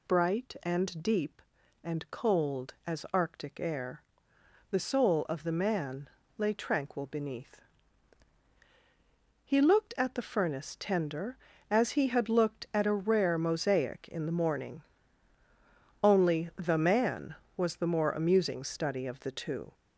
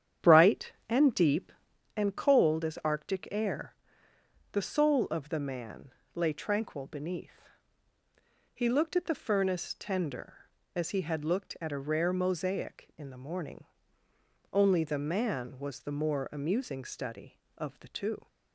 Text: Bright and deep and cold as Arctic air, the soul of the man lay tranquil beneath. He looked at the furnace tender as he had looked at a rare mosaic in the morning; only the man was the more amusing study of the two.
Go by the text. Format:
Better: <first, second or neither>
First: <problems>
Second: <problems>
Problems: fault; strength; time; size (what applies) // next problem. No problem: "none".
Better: first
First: pauses between "man" and "lay"; slight; at 6.0 s; 0.30 s long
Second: starts louder than the rest; strong; until 1.8 s; 9 dB // pauses between "man" and "lay"; slight; at 5.9 s; 0.22 s long